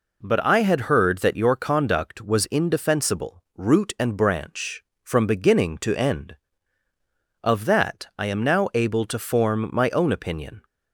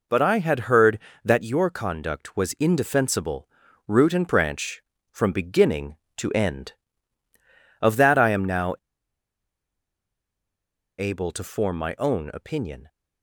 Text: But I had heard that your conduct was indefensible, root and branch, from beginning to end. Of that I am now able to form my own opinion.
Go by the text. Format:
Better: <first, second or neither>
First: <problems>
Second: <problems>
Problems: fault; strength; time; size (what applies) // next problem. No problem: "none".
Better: first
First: none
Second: pauses between "now" and "able"; strong; at 8.7 s; 2.2 s long